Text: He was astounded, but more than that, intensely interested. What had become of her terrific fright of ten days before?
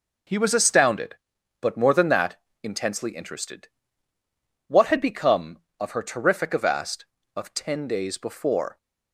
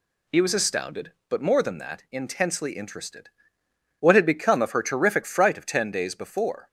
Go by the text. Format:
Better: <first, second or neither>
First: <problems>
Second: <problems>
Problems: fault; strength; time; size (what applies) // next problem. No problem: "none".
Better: second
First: says "avast" for "fright"; at 6.5 s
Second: none